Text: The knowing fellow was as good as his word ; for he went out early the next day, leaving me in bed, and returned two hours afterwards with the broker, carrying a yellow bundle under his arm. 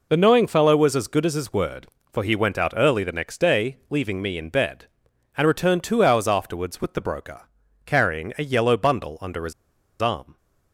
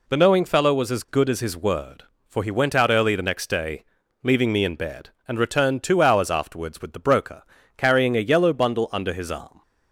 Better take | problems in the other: second | pauses between "his" and "arm"; noticeable; at 9.5 s; 0.49 s long

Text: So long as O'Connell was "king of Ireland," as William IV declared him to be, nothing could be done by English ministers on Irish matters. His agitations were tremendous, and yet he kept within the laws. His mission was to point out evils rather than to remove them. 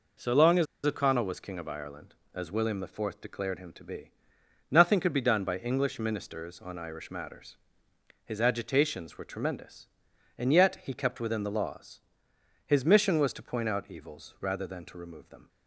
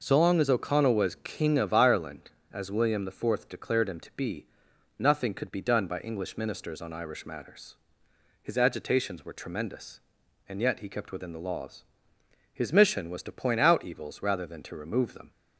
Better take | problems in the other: second | pauses between "as" and "O'Connell"; slight; at 0.6 s; 0.20 s long

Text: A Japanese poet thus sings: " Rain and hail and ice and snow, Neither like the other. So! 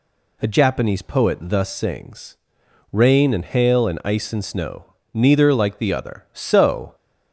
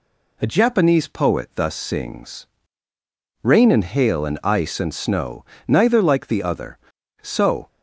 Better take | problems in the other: first | changes voice at "Japanese"; from 0.4 s on; 7.2 s long

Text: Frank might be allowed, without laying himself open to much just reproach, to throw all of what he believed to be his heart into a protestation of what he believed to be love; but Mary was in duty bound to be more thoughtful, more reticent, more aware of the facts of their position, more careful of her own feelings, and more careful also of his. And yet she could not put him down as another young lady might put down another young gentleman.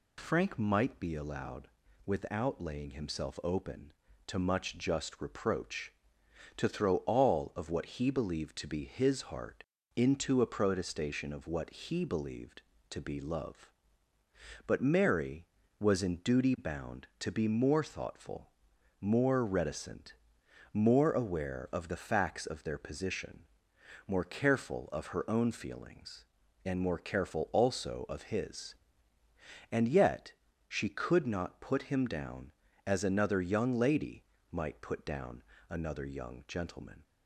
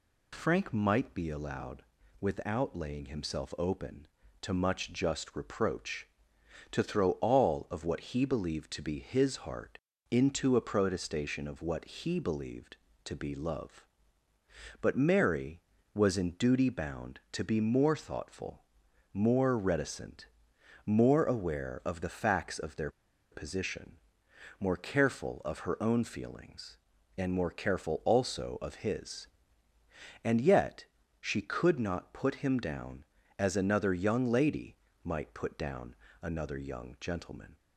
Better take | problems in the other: first | pauses between "heart" and "into"; slight; at 9.7 s; 0.32 s long; slight in the first // pauses between "their" and "position"; at 22.8 s; 0.41 s long // pauses between "yet" and "she"; slight; at 30.8 s; 0.36 s long; slight in the first // pauses between "lady" and "might"; slight; at 34.7 s; 0.28 s long; slight in the first // pauses between "down" and "another"; slight; at 35.9 s; 0.26 s long; slight in the first

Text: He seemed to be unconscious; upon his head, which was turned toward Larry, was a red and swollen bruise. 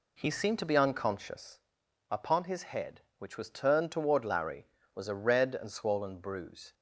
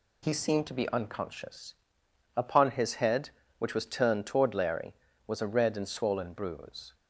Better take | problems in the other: second | starts louder than the rest; slight; until 1.6 s; 2.5 dB

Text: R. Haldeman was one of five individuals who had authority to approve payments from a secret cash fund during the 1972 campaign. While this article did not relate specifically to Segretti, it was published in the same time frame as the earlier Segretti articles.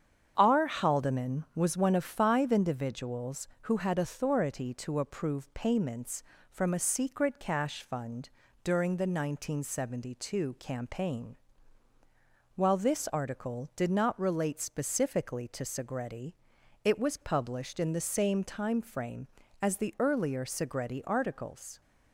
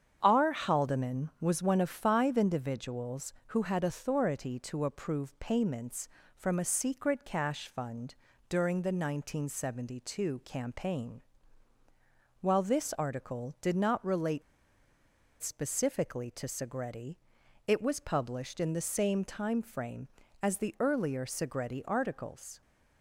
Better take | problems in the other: first | starts louder than the rest; strong; until 1.2 s; 8 dB; strong in the first // pauses between "fund" and "during"; slight; at 8.1 s; 0.34 s long; slight in the first // pauses between "relate" and "specifically"; at 14.4 s; 1.0 s long

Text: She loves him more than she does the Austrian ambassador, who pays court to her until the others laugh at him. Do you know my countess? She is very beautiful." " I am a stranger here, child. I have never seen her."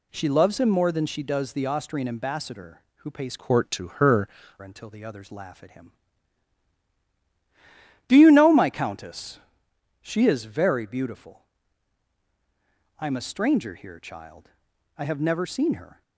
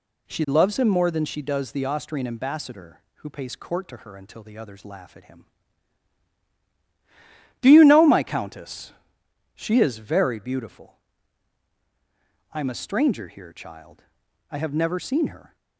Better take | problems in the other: second | changes voice from "court" to "her"; from 3.3 to 4.2 s; 0.9 s long

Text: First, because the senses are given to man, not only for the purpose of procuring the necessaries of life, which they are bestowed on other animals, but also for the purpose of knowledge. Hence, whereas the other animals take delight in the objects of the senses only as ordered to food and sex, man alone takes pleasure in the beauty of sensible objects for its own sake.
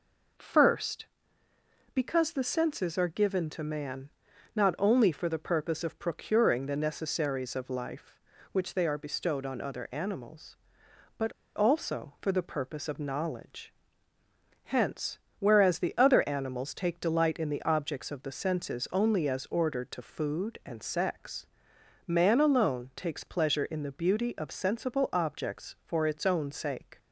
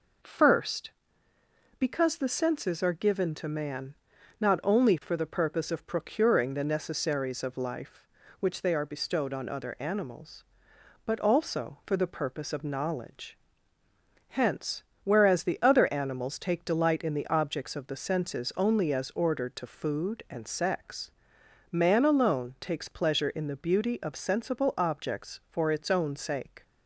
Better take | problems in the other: second | pauses between "but" and "also"; slight; at 11.3 s; 0.23 s long

